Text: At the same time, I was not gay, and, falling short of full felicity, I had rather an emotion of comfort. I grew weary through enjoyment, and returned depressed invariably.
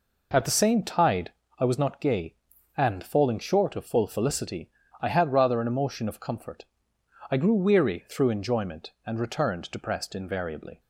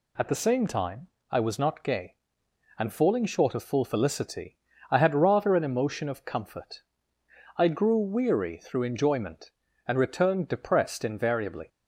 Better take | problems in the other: second | says "tide" for "time"; at 0.8 s

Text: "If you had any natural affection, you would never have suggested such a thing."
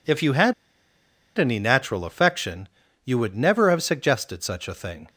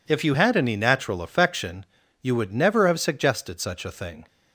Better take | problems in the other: second | pauses between "had" and "any"; noticeable; at 0.5 s; 0.83 s long

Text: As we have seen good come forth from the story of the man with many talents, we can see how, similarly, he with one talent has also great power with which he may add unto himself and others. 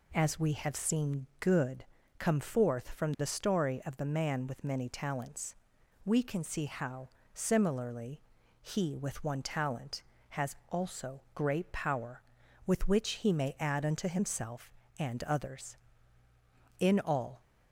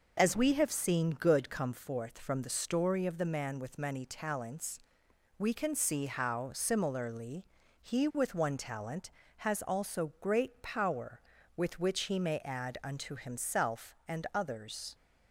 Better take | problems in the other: second | pauses between "good" and "come"; slight; at 1.8 s; 0.34 s long // goes on to say "In all"; from 16.8 s on; 0.60 s long

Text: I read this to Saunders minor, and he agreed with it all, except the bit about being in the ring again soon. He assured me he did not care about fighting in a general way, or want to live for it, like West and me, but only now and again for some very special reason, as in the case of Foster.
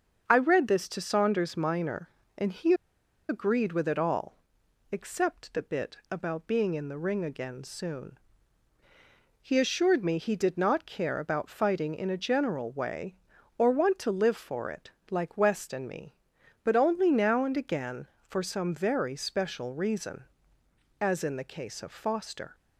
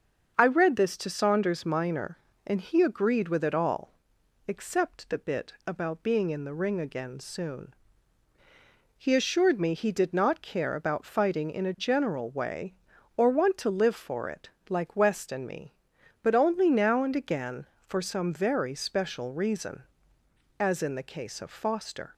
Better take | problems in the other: second | starts louder than the rest; until 1.2 s; 7 dB; also in the second // pauses between "he" and "agreed"; noticeable; at 2.7 s; 0.55 s long

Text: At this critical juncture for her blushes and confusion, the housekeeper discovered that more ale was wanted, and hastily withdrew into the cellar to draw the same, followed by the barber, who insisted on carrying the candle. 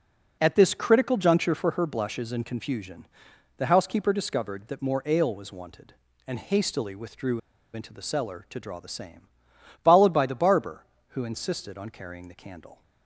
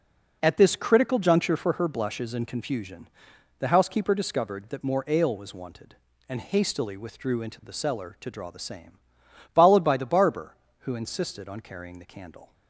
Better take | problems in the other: second | pauses between "withdrew" and "into"; slight; at 7.4 s; 0.33 s long

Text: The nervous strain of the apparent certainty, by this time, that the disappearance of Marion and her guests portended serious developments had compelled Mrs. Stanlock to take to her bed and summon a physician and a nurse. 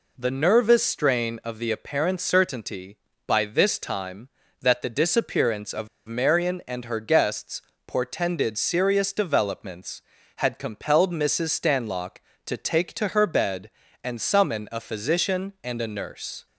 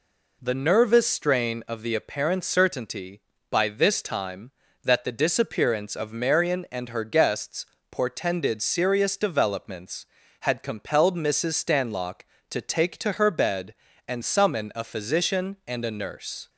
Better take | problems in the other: second | pauses between "of" and "Marion"; slight; at 5.8 s; 0.19 s long // pauses between "guests" and "portended"; slight; at 7.6 s; 0.24 s long; slight in the second

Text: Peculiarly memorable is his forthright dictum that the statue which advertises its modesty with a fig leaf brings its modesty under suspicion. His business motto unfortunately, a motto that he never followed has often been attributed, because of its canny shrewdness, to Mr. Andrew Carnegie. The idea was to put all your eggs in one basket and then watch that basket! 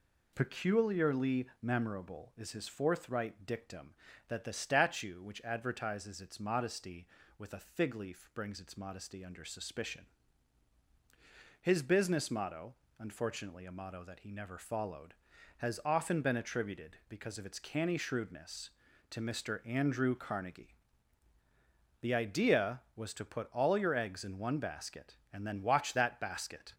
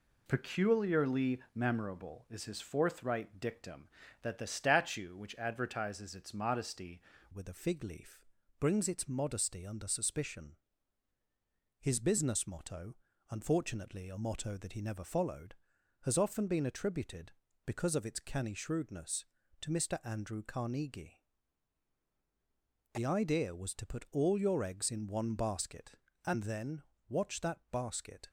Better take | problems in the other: first | changes voice at "with"; from 7.3 s on; 20.9 s long // pauses between "leaf" and "brings"; slight; at 8.2 s; 0.36 s long // pauses between "motto" and "unfortunately"; slight; at 12.9 s; 0.34 s long; slight in the first // pauses between "then" and "watch"; slight; at 26.8 s; 0.28 s long

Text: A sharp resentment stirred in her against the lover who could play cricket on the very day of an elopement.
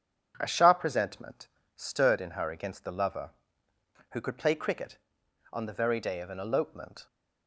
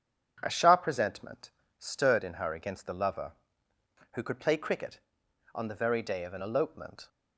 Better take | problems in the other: neither | starts louder than the rest; strong; the same in both // pauses between "resentment" and "stirred"; slight; the same in both

